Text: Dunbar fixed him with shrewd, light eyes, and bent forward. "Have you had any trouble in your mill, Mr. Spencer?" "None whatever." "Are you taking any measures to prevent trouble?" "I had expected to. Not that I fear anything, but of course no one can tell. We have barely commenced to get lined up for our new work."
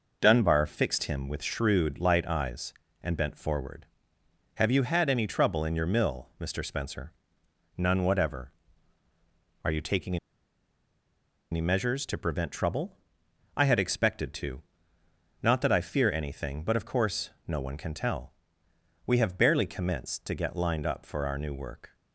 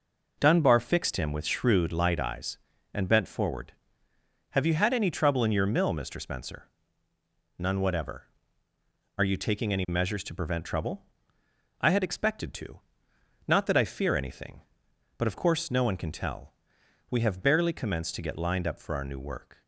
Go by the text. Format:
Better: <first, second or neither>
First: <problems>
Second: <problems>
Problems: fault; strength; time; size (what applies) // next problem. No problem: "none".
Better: second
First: pauses between "taking" and "any"; strong; at 10.1 s; 1.3 s long // pauses between "course" and "no"; slight; at 17.3 s; 0.16 s long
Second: none